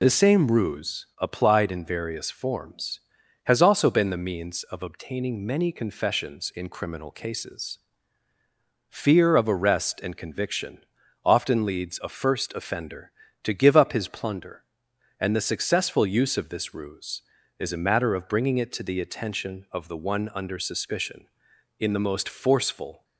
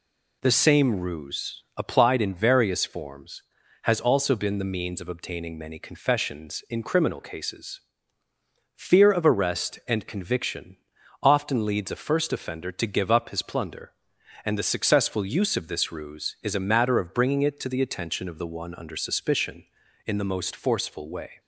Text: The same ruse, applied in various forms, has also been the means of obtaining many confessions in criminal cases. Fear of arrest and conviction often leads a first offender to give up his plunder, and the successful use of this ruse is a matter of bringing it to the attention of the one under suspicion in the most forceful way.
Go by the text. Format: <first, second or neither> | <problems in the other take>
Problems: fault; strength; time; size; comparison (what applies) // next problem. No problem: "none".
second | pauses between "conviction" and "often"; at 10.8 s; 0.44 s long; noticeable in the second // stops before "way"; at 23.0 s